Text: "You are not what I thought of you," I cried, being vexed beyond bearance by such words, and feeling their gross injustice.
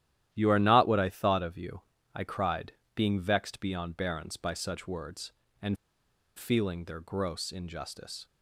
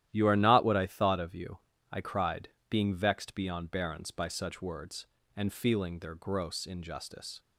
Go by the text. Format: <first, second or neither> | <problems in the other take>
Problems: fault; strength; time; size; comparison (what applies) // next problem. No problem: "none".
second | starts louder than the rest; strong; until 1.3 s; 12.5 dB; strong in the second // pauses between "and" and "feeling"; noticeable; at 5.7 s; 0.61 s long